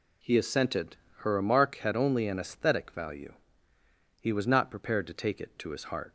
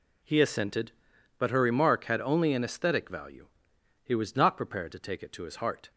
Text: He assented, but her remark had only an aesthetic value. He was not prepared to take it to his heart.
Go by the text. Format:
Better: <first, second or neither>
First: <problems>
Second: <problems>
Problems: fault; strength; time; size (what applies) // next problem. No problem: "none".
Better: second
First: skips "but"; at 1.0 s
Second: none